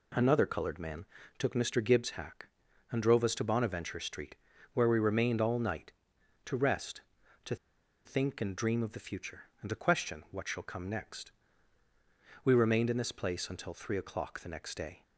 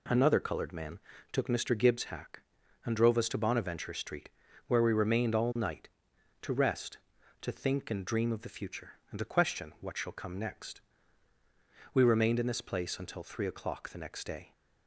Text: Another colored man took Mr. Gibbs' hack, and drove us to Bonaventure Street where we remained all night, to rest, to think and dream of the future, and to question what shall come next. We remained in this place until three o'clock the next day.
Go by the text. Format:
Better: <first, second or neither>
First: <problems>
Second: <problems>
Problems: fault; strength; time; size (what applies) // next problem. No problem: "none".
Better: second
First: pauses between "man" and "took"; slight; at 1.0 s; 0.34 s long // pauses between "Street" and "where"; at 4.3 s; 0.40 s long // pauses between "to" and "think"; noticeable; at 7.5 s; 0.50 s long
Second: pauses between "man" and "took"; slight; at 0.9 s; 0.34 s long // pauses between "Street" and "where"; at 4.2 s; 0.40 s long